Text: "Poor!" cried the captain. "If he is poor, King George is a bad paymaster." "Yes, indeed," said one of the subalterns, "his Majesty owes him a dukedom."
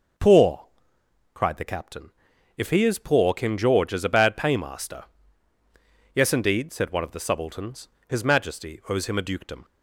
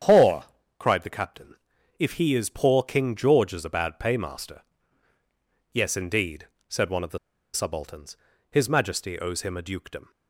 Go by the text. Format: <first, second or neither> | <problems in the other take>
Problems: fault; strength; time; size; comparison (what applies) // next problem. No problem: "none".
first | starts louder than the rest; strong; until 1.3 s; 8.5 dB // pauses between "the" and "subalterns"; at 7.1 s; 0.37 s long